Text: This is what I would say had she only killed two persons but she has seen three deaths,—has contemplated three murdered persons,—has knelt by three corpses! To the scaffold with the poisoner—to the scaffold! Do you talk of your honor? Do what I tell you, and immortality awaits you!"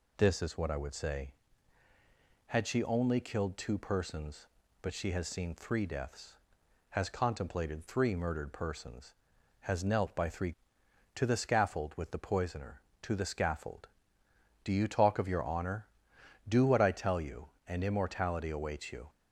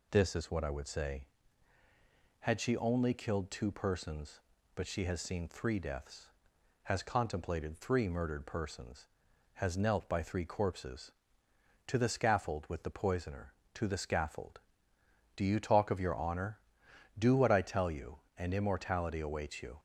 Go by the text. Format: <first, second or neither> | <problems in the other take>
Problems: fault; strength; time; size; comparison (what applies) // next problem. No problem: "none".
second | skips "corpses"; at 10.8 s